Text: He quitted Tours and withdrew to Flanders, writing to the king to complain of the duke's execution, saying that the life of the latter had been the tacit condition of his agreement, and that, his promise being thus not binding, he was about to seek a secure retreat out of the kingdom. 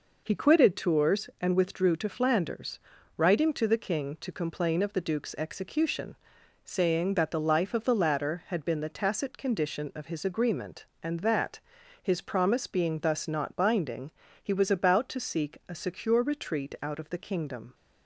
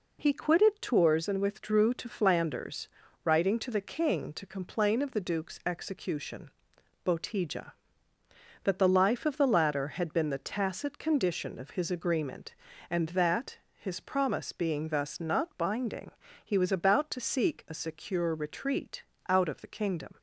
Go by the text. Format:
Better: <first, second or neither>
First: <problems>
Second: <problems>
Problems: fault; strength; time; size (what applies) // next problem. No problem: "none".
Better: first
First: none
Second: says "botija" for "saying"; at 7.0 s // pauses between "retreat" and "out"; slight; at 19.0 s; 0.26 s long